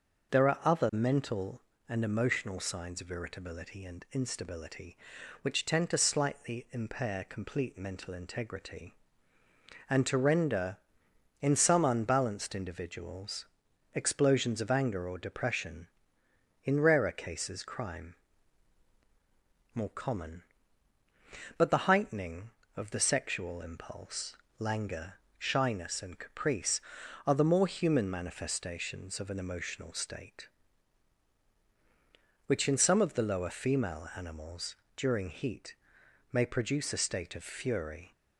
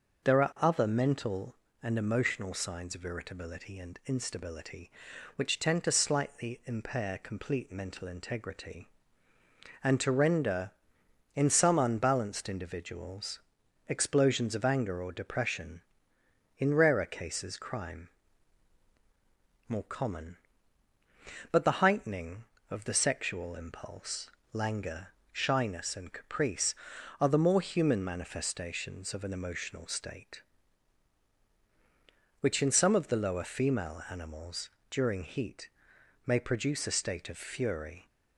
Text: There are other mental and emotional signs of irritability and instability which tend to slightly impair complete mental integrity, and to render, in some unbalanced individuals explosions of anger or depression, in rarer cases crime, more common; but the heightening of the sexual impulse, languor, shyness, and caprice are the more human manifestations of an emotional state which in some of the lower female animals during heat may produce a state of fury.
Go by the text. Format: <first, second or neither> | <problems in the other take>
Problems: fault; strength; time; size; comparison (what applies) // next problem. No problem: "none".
neither | starts louder than the rest; the same in both // pauses between "individuals" and "explosions"; noticeable; the same in both // pauses between "animals" and "during"; slight; the same in both // pauses between "heat" and "may"; noticeable; the same in both